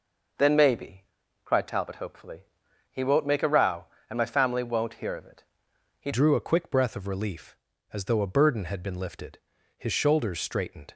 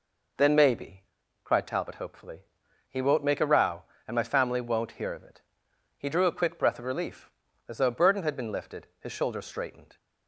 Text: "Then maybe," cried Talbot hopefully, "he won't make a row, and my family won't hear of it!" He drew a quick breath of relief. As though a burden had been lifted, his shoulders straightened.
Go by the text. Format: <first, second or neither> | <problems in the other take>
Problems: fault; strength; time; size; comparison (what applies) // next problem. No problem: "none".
second | changes voice at "drew"; from 6.1 s on; 4.8 s long